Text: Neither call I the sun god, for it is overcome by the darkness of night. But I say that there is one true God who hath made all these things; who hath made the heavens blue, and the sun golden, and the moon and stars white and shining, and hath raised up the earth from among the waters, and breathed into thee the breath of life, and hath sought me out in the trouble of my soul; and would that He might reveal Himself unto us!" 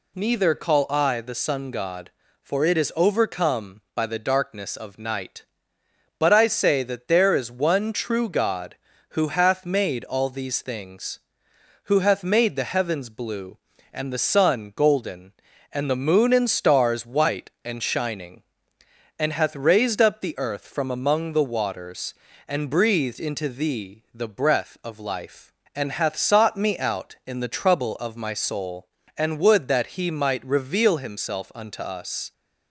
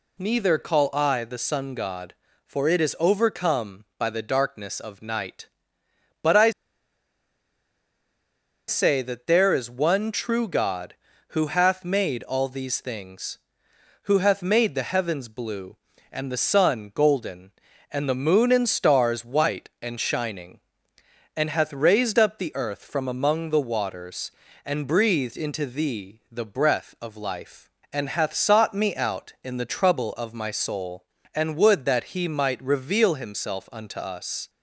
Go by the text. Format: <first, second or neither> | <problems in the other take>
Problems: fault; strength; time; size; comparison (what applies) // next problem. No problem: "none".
first | pauses between "I" and "say"; strong; at 6.5 s; 2.1 s long